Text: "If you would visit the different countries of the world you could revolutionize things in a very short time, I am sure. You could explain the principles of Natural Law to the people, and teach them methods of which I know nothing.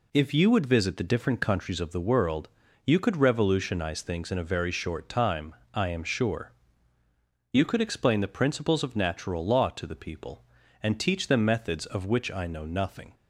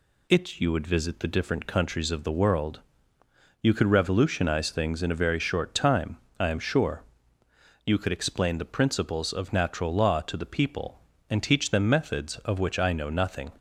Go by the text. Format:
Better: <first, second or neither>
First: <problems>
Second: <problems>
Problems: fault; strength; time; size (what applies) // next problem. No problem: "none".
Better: first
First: pauses between "world" and "you"; slight; at 2.4 s; 0.36 s long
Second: says "It" for "If"; at 0.3 s // pauses between "world" and "you"; noticeable; at 2.8 s; 0.80 s long